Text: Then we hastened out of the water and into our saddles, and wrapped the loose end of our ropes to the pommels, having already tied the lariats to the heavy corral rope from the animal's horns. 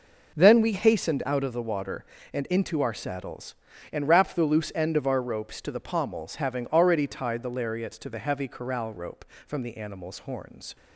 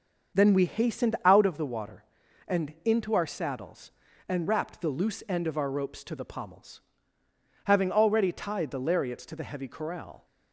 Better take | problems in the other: first | starts louder than the rest; until 1.4 s; 6.5 dB // stops before "rope from the animal's horns"; at 10.2 s

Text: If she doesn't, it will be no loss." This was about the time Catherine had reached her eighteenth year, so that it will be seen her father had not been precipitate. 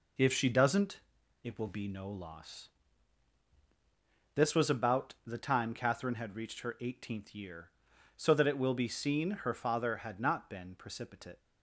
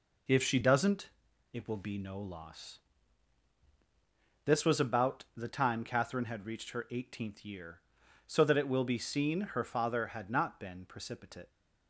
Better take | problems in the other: neither | none

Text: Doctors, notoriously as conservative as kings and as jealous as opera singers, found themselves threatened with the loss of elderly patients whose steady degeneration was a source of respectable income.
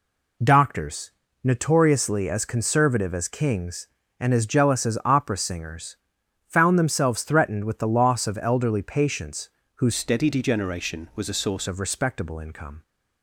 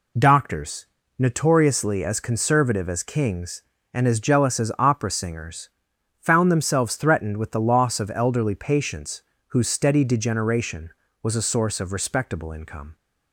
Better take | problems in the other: second | pauses between "patients" and "whose"; slight; at 9.4 s; 0.28 s long; slight in the second // changes voice from "steady" to "source"; from 9.9 to 11.6 s; 1.7 s long

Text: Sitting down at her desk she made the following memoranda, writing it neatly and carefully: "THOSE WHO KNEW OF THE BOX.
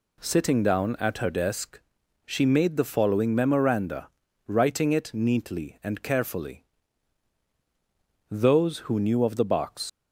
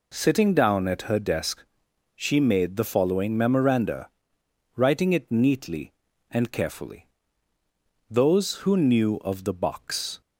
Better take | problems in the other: second | pauses between "desk" and "she"; noticeable; at 1.7 s; 0.46 s long; noticeable in the second // leaves "BOX" unfinished; at 9.8 s; 110 ms

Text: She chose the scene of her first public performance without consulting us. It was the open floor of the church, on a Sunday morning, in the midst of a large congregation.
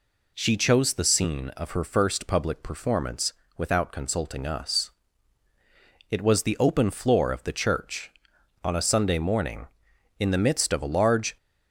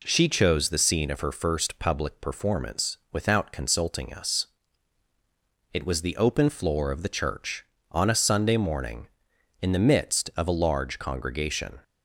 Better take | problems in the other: second | pauses between "performance" and "without"; slight; at 3.3 s; 0.24 s long; slight in the second // stops before "congregation"; at 11.3 s

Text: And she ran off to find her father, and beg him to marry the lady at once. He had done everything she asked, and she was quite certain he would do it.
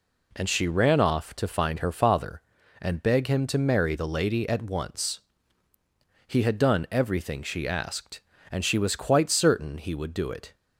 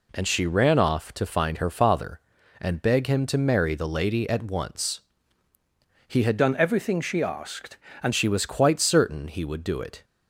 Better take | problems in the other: first | changes voice from "done" to "and"; from 6.3 to 8.1 s; 1.8 s long

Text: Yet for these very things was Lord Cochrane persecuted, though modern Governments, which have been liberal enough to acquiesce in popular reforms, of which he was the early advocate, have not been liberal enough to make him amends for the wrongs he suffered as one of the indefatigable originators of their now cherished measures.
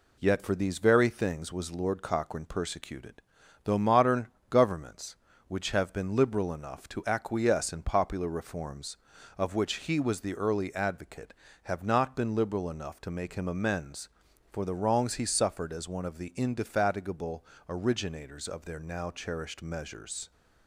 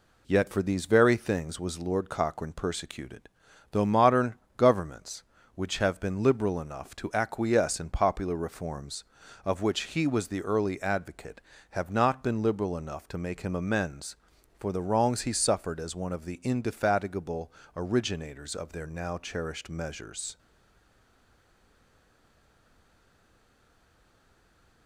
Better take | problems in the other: first | pauses between "modern" and "Governments"; slight; at 4.3 s; 0.22 s long; slight in the first // pauses between "indefatigable" and "originators"; slight; at 17.5 s; 0.24 s long; slight in the first // stays silent after the last word; strong; from 20.3 s on; 4.5 s long

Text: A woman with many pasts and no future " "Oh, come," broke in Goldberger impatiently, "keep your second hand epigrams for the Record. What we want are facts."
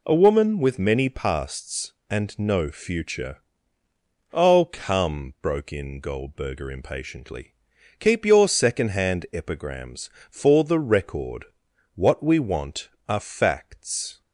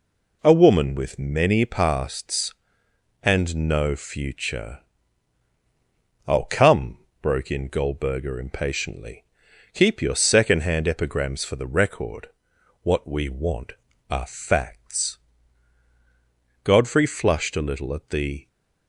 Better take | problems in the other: first | goes on to say "Godfrey flushed a little at the"; strong; from 16.6 s on; 1.8 s long

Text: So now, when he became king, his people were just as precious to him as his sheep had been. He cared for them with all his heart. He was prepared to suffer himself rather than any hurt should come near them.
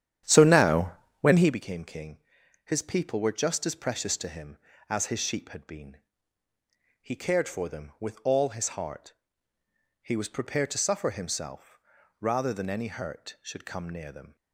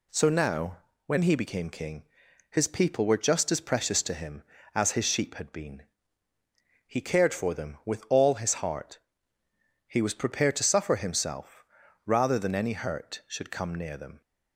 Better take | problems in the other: second | starts louder than the rest; strong; until 1.6 s; 10 dB // pauses between "himself" and "rather"; at 11.7 s; 0.44 s long; also in the second

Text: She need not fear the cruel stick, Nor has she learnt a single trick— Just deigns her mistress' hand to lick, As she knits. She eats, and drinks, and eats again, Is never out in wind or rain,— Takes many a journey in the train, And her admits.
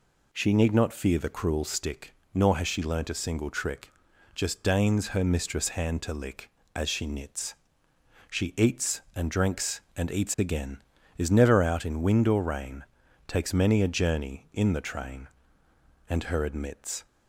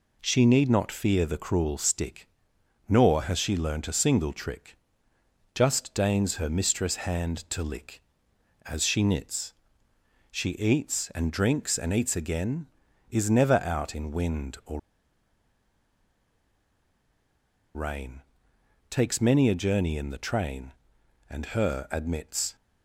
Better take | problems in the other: first | pauses between "or" and "rain"; strong; at 14.7 s; 2.9 s long

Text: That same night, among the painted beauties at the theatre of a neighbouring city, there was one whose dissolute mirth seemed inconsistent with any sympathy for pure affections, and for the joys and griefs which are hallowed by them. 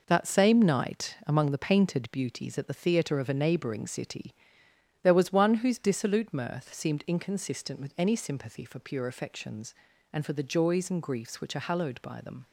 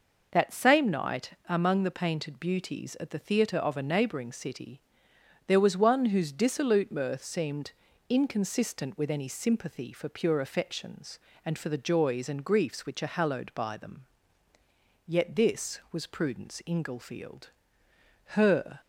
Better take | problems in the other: first | pauses between "seemed" and "inconsistent"; at 7.7 s; 0.38 s long // goes on to say "Yet this was Prudence Inglefield Her"; strong; from 15.0 s on; 3.7 s long

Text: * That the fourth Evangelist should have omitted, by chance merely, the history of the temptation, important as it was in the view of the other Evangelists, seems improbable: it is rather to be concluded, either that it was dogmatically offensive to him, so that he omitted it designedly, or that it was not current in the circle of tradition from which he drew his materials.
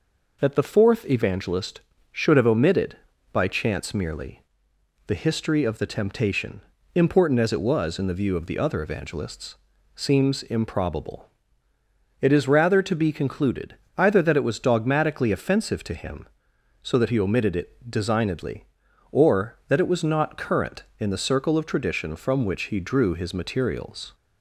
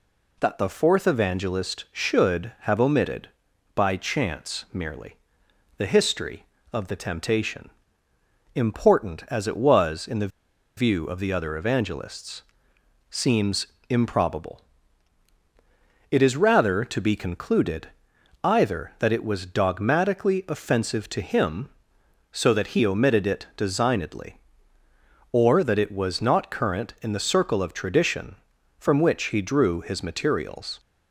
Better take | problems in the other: first | pauses between "the" and "view"; noticeable; at 10.2 s; 0.49 s long // pauses between "seems" and "improbable"; slight; at 13.6 s; 0.22 s long

